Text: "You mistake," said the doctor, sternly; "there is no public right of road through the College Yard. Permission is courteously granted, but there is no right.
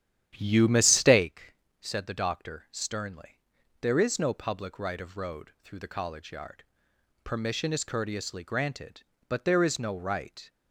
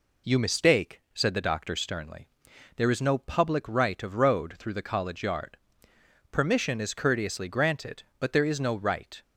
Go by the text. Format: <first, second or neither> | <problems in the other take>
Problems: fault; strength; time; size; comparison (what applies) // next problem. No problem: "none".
second | starts louder than the rest; strong; until 1.3 s; 10.5 dB